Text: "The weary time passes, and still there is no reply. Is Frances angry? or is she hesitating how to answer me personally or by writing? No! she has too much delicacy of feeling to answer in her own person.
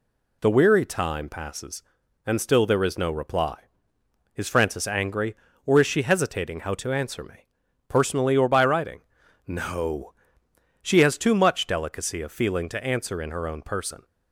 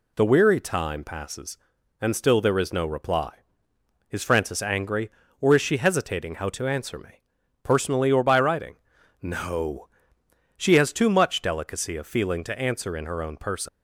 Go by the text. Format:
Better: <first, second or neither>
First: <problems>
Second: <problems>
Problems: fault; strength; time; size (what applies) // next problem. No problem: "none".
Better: first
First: pauses between "me" and "personally"; at 7.4 s; 0.42 s long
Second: pauses between "me" and "personally"; at 7.2 s; 0.42 s long // leaves "person" unfinished; at 13.6 s; 105 ms